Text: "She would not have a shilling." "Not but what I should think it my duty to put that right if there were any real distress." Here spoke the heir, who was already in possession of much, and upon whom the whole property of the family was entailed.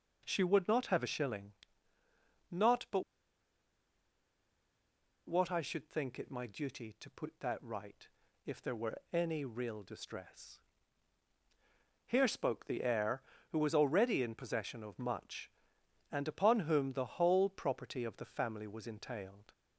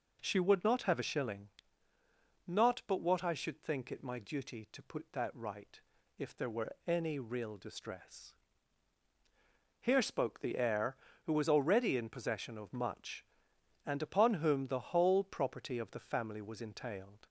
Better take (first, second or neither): second